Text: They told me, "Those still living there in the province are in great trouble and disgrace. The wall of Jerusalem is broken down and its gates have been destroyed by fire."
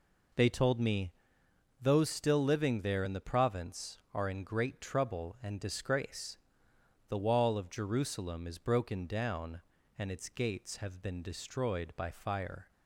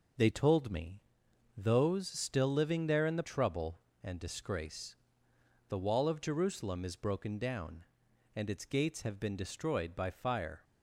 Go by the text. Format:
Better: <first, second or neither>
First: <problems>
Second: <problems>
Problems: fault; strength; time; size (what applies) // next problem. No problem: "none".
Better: first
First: none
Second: skips "province are in great"; at 3.2 s